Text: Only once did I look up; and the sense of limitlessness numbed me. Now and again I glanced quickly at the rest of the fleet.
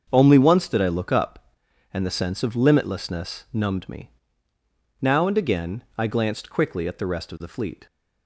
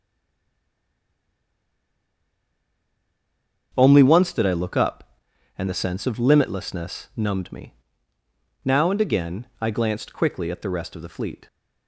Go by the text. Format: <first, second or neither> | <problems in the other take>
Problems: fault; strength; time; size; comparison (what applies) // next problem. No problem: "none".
first | stays silent before the first word; strong; until 3.7 s; 3.7 s long // starts louder than the rest; until 4.7 s; 7 dB; also in the first